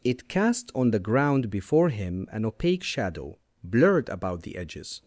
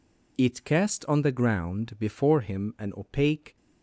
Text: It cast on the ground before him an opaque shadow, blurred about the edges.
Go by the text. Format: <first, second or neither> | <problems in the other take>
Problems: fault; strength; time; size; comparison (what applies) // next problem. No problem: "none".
first | stops before "shadow blurred about the edges"; at 3.5 s